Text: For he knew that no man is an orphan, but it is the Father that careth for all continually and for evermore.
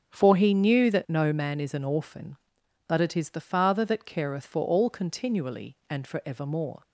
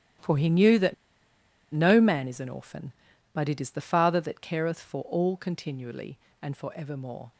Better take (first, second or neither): first